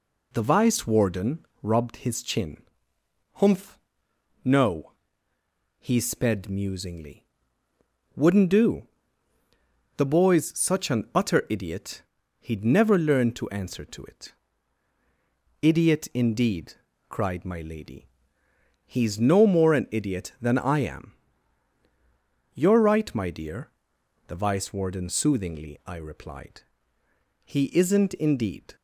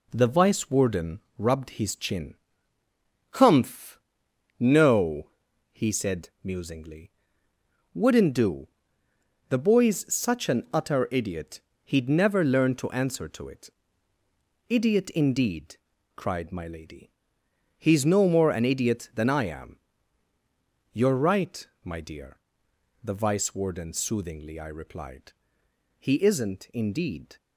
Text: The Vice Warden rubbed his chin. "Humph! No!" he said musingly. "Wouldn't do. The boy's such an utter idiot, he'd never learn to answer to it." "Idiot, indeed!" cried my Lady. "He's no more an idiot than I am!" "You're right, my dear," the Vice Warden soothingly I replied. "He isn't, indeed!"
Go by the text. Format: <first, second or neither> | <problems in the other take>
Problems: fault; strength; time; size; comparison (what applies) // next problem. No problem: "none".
second | pauses between "Warden" and "rubbed"; slight; at 1.4 s; 0.16 s long; slight in the second // says "sped" for "said"; at 5.9 s